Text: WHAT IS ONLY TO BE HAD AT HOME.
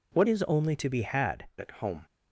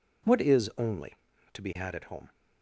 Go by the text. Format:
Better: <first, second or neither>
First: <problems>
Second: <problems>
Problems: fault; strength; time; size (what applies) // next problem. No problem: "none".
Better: second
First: changes voice from "IS" to "HAD"; from 0.2 to 1.4 s; 1.2 s long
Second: none